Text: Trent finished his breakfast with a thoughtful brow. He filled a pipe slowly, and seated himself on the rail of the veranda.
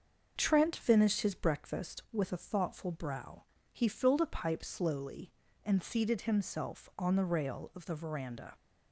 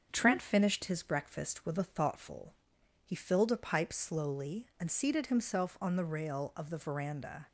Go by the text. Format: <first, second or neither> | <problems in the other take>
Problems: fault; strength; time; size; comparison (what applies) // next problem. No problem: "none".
first | starts louder than the rest; until 1.1 s; 7 dB; also in the first // skips "brow"; at 2.7 s